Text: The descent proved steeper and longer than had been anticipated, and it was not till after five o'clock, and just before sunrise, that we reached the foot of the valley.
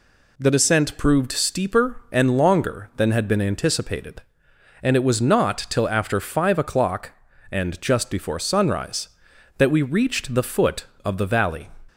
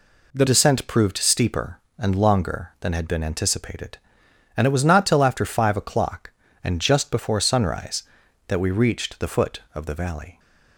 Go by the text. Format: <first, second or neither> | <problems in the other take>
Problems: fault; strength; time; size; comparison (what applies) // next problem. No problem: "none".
first | changes voice at "descent"; from 0.4 s on; 9.9 s long